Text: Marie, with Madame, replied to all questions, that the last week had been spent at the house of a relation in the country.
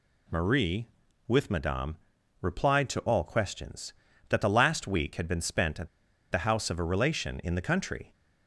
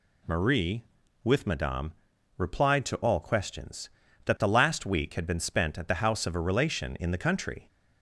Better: second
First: pauses between "at" and "the"; at 5.8 s; 0.43 s long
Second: none

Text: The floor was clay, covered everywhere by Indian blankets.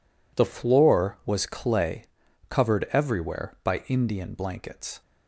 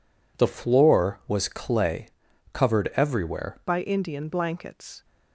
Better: first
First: none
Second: changes voice at "by"; from 3.6 s on; 1.4 s long

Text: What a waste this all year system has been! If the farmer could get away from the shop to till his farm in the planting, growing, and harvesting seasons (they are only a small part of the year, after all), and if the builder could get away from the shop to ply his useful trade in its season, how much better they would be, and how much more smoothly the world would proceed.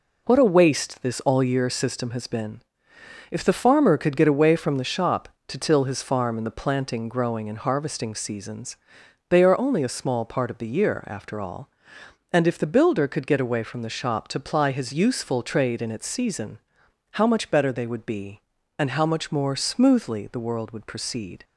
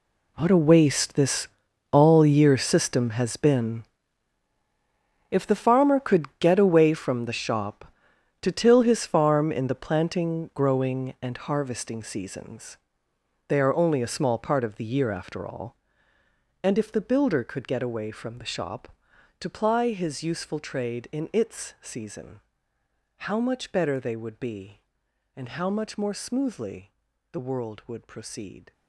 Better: first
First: none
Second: gets quieter; strong; throughout; 15 dB // pauses between "this" and "all"; noticeable; at 1.4 s; 0.46 s long // pauses between "smoothly" and "the"; at 26.9 s; 0.40 s long

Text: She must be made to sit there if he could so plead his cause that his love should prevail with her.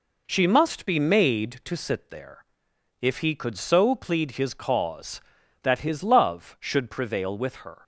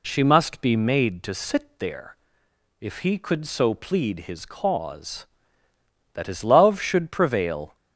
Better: first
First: pauses between "there" and "if"; noticeable; at 2.4 s; 0.56 s long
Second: pauses between "there" and "if"; noticeable; at 2.1 s; 0.64 s long // stops before "with her"; at 7.7 s

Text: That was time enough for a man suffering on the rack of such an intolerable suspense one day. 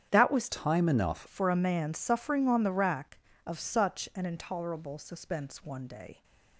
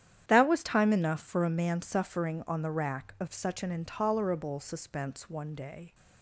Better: second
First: starts louder than the rest; strong; until 1.1 s; 9.5 dB // changes voice from "time" to "enough"; from 0.4 to 1.2 s; 0.8 s long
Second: starts louder than the rest; strong; until 1.2 s; 10 dB

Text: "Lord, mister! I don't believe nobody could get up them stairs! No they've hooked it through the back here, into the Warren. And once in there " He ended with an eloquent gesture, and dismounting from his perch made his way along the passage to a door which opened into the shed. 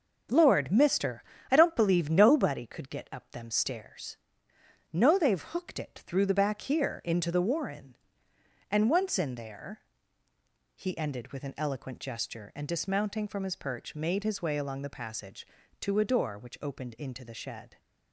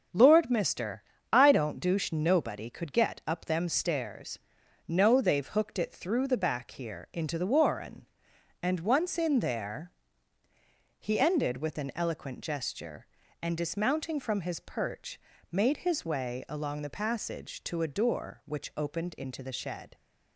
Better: first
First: none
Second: starts louder than the rest; until 1.4 s; 6.5 dB // says "douche" for "believe"; at 1.7 s // pauses between "perch" and "made"; slight; at 15.2 s; 0.32 s long

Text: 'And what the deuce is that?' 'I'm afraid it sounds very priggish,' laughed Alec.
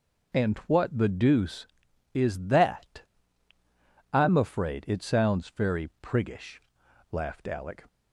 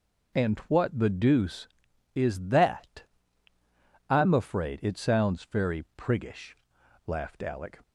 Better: neither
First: none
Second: none

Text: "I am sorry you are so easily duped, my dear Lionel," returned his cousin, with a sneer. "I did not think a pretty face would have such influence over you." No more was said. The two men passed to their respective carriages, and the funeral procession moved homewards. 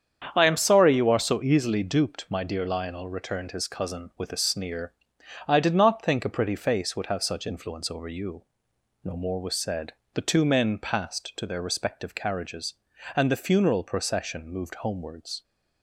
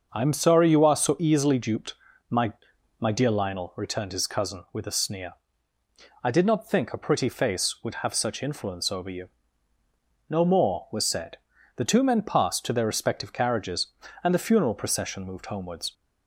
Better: first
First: starts louder than the rest; strong; until 1.3 s; 7.5 dB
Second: starts louder than the rest; until 1.1 s; 6 dB // says "my" twice; at 2.9 s

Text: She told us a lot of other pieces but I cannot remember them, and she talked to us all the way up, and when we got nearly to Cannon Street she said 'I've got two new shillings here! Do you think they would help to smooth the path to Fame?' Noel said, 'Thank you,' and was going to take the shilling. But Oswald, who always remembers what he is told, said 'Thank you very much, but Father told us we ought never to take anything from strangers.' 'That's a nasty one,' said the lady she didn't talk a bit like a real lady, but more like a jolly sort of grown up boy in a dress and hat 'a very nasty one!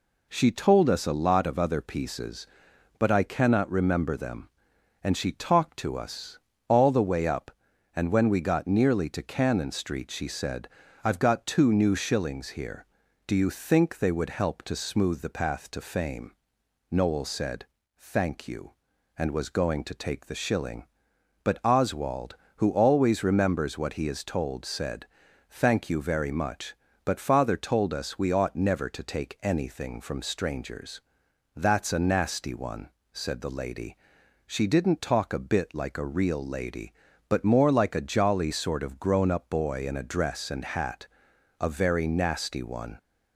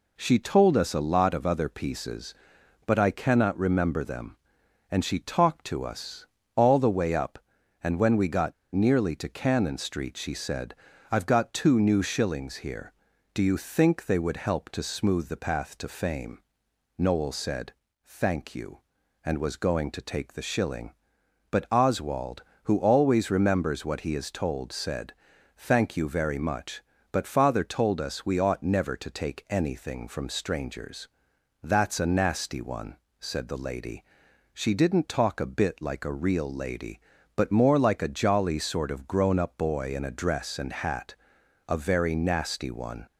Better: first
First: pauses between "us" and "all"; slight; at 6.3 s; 0.30 s long // pauses between "said" and "I've"; at 10.6 s; 0.37 s long // pauses between "said" and "Thank"; at 25.0 s; 0.44 s long // pauses between "lady" and "she"; noticeable; at 33.9 s; 0.54 s long // pauses between "hat" and "a"; noticeable; at 41.0 s; 0.54 s long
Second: pauses between "us" and "all"; slight; at 6.2 s; 0.30 s long // pauses between "got" and "nearly"; slight; at 8.5 s; 0.19 s long // pauses between "said" and "I've"; at 10.7 s; 0.38 s long // pauses between "said" and "Thank"; at 25.1 s; 0.44 s long // pauses between "lady" and "she"; noticeable; at 34.0 s; 0.54 s long // pauses between "hat" and "a"; noticeable; at 41.1 s; 0.54 s long

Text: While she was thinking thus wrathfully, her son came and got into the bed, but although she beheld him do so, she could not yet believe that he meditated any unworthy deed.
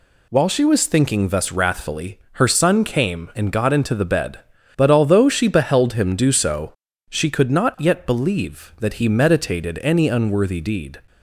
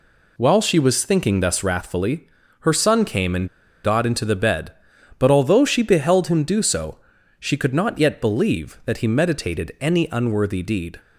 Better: first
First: none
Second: pauses between "and" and "got"; at 3.4 s; 0.36 s long

